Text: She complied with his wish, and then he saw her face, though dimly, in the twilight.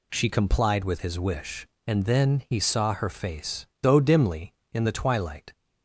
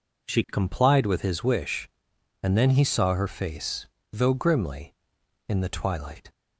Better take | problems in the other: first | says "grimly" for "dimly"; at 4.3 s

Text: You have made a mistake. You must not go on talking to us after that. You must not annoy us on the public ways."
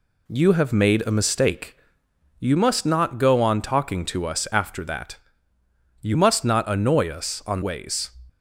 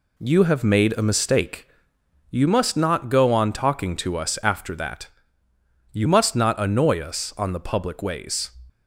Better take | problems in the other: second | skips "the public"; at 7.6 s

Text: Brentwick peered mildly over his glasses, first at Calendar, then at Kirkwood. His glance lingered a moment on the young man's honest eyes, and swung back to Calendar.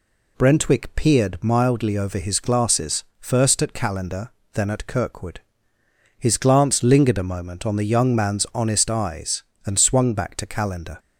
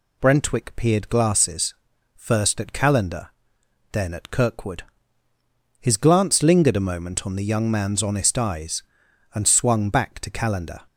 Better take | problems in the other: first | skips "mildly over his"; at 1.0 s

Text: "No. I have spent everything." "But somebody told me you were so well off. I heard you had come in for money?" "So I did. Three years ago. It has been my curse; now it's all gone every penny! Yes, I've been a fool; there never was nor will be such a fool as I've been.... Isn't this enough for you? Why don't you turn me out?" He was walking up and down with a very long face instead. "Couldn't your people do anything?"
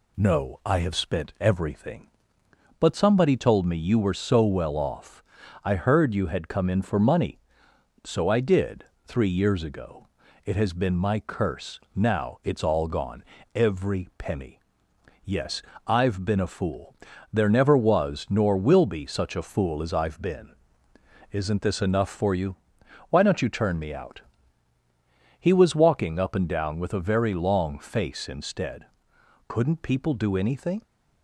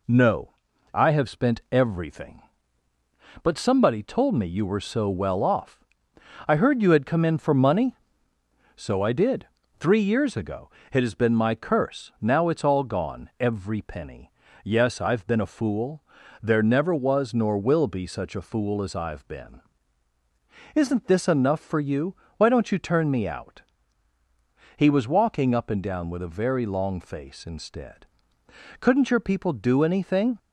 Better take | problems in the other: second | pauses between "gone" and "every"; slight; at 13.2 s; 0.30 s long // skips "your"; at 29.8 s

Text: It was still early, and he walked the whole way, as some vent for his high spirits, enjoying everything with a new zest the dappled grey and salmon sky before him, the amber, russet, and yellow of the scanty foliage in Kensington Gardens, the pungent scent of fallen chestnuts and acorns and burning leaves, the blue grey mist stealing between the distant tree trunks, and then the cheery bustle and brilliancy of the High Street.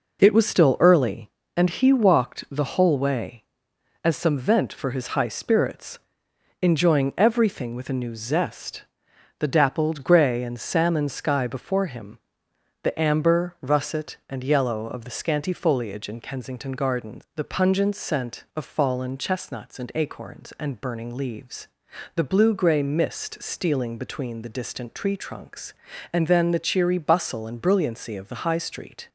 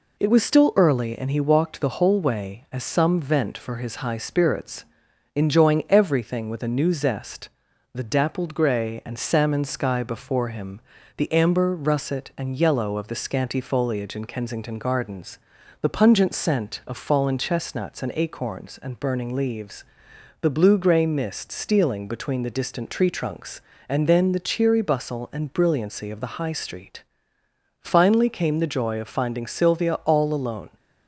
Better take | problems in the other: first | pauses between "zest" and "the"; noticeable; at 7.4 s; 0.46 s long; noticeable in the first // goes on to say "Finally came the joy of finding Sylvia all alone"; strong; from 27.7 s on; 2.9 s long

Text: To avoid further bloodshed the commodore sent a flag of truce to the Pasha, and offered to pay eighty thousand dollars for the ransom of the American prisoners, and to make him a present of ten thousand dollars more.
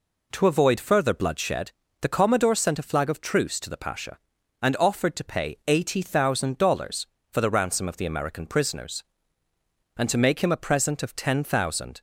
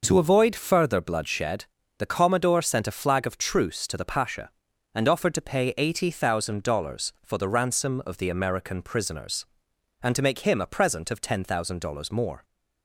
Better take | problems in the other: second | pauses between "bloodshed" and "the"; slight; at 1.7 s; 0.30 s long; slight in the second // stops before "dollars more"; at 11.9 s

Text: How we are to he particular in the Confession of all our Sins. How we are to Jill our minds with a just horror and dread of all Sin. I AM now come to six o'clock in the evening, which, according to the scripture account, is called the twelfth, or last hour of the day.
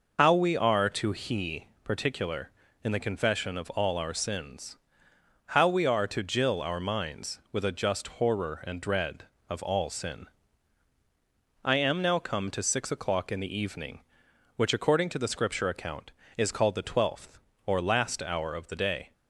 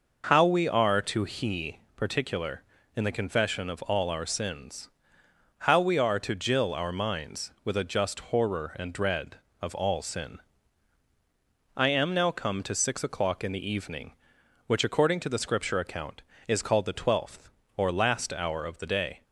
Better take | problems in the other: second | loses the start of "How"; at 0.1 s; 65 ms // pauses between "he" and "particular"; slight; at 1.6 s; 0.20 s long; slight in the second

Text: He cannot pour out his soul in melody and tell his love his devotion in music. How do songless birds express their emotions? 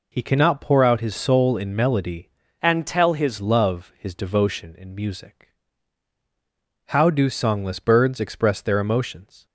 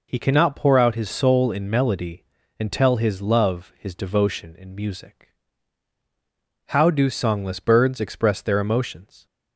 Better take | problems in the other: second | changes voice from "and" to "his"; from 2.6 to 3.3 s; 0.7 s long

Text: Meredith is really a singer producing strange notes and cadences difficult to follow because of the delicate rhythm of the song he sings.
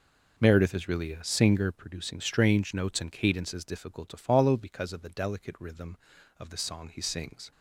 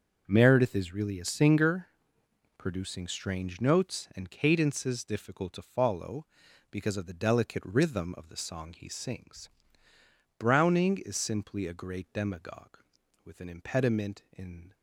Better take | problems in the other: first | starts louder than the rest; until 1.2 s; 6.5 dB // pauses between "singer" and "producing"; noticeable; at 1.8 s; 0.70 s long // goes on to say "Browning is simply a great demagogue with an impediment in"; strong; from 10.3 s on; 4.3 s long

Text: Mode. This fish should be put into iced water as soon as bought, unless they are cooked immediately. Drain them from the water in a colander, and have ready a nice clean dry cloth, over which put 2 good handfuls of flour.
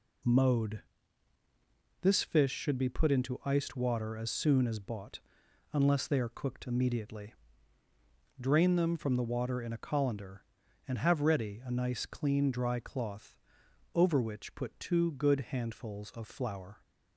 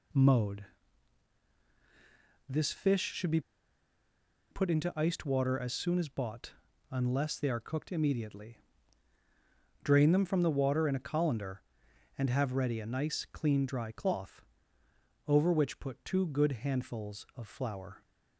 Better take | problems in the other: first | pauses between "be" and "put"; at 3.3 s; 1.1 s long

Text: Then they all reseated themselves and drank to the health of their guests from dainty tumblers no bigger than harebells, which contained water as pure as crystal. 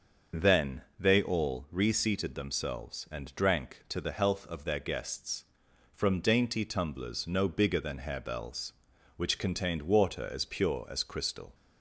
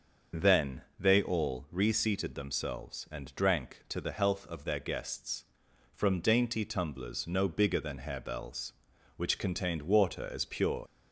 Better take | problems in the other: first | starts louder than the rest; until 1.5 s; 6.5 dB; also in the first // pauses between "Then" and "they"; slight; at 0.8 s; 0.16 s long; slight in the first // stops before "as crystal"; at 10.8 s

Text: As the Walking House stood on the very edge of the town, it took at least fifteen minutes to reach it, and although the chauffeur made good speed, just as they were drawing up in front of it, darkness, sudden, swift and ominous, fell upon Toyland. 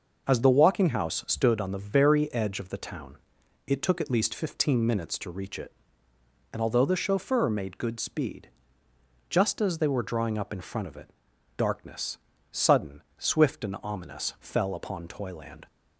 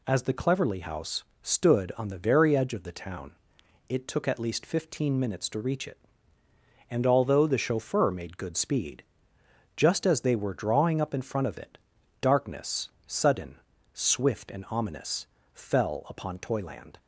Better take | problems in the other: first | says "Cleverly" for "Walking"; at 0.3 s // pauses between "House" and "stood"; slight; at 1.2 s; 0.22 s long

